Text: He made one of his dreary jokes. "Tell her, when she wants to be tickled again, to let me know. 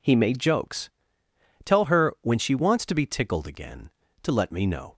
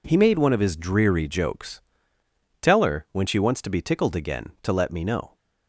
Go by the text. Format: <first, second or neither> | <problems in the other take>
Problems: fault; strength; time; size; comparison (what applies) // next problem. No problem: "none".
second | skips "one of his dreary"; at 0.3 s